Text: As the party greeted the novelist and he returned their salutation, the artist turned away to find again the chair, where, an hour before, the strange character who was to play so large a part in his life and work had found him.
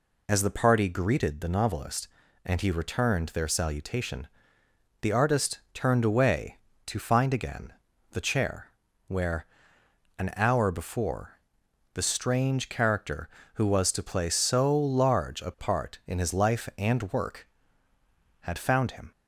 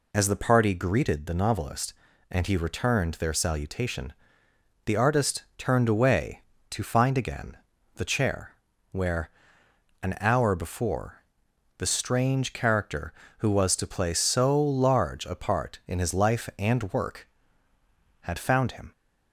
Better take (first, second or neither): neither